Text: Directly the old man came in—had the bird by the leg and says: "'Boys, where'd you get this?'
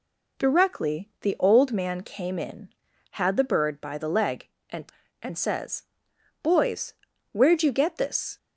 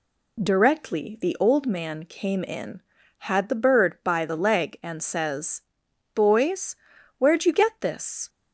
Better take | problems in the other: second | says "and" twice; at 5.2 s

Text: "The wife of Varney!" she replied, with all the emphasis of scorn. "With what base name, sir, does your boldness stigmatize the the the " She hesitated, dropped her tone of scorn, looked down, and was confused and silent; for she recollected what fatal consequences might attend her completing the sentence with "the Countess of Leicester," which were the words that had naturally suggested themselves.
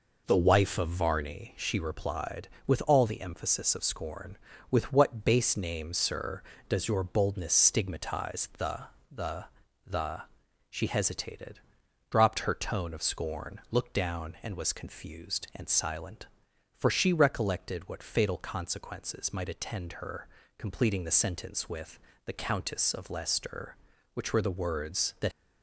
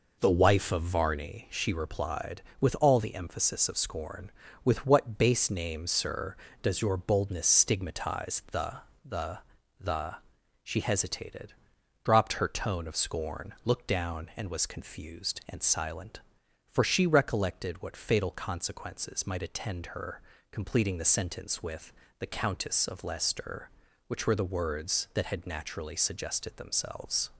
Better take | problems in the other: second | pauses between "the" and "the"; slight; at 8.8 s; 0.24 s long; slight in the second // pauses between "the" and "the"; at 9.4 s; 0.40 s long; also in the second // pauses between "her" and "completing"; slight; at 20.2 s; 0.30 s long; slight in the second // pauses between "with" and "the"; slight; at 21.9 s; 0.26 s long; slight in the second // stops before "had naturally suggested themselves"; at 25.3 s

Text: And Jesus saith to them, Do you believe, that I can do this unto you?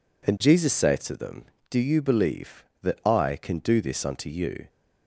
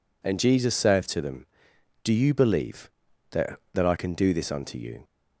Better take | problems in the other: first | says "that" twice; at 3.7 s

